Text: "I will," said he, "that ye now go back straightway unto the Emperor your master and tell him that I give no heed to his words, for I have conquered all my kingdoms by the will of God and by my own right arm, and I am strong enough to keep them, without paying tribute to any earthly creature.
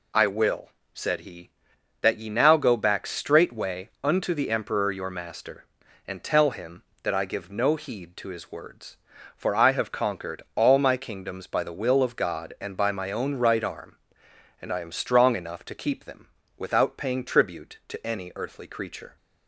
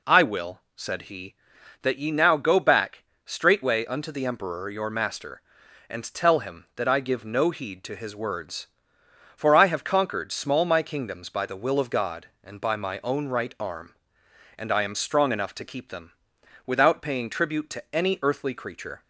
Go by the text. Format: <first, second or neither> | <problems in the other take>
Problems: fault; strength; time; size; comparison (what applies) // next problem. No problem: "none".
first | pauses between "back" and "straightway"; slight; at 3.0 s; 0.20 s long // says "small" for "all"; at 10.3 s